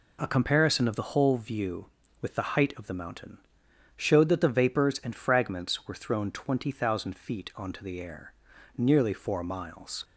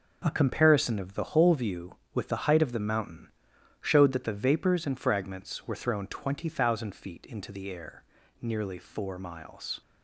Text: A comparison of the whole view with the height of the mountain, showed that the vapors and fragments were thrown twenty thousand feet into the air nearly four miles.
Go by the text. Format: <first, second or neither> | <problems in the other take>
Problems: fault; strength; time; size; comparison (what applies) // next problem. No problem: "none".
second | says "onto" for "into"; at 7.5 s // pauses between "air" and "nearly"; at 8.3 s; 0.42 s long; slight in the second